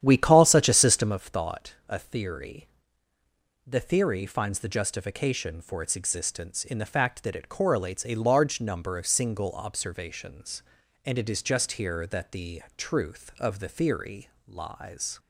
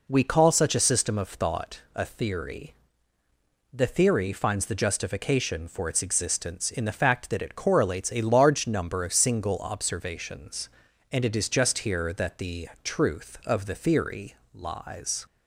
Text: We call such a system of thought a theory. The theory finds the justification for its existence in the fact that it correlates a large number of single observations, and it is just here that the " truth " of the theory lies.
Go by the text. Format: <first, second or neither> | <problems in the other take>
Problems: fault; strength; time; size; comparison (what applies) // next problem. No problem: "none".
second | starts louder than the rest; strong; until 1.2 s; 10 dB // pauses between "thought" and "a"; slight; at 1.7 s; 0.16 s long; slight in the second // pauses between "theory" and "lies"; slight; at 14.2 s; 0.18 s long; slight in the second